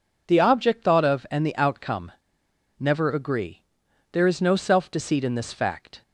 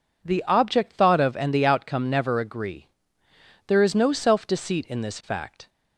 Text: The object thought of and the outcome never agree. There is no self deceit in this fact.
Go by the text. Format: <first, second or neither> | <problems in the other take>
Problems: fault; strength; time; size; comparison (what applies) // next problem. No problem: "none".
second | pauses between "outcome" and "never"; noticeable; at 2.1 s; 0.65 s long